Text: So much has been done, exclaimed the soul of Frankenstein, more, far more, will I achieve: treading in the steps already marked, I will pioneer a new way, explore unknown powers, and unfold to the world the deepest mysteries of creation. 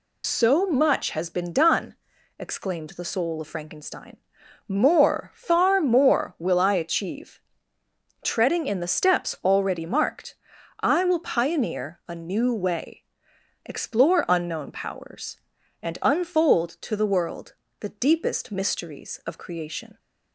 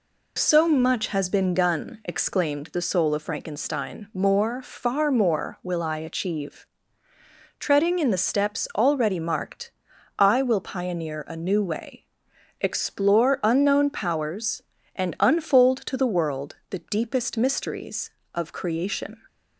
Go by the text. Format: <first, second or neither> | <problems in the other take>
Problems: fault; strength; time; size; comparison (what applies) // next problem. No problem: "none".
second | loses the start of "So"; at 0.2 s; 90 ms // pauses between "world" and "the"; slight; at 17.5 s; 0.26 s long